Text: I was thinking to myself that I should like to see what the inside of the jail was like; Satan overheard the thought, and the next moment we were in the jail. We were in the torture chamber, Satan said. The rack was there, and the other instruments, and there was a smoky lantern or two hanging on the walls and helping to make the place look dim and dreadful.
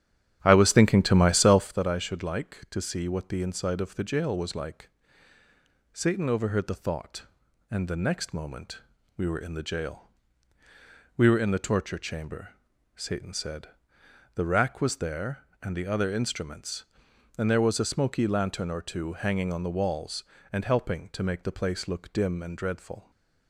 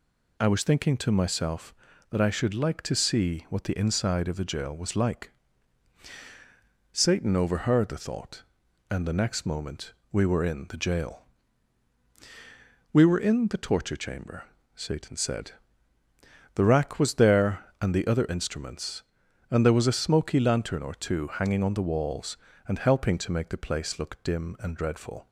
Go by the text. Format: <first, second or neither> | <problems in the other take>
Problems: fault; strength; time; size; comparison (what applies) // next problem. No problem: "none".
second | starts louder than the rest; strong; until 1.9 s; 10.5 dB // pauses between "moment" and "we"; at 8.7 s; 0.38 s long; slight in the second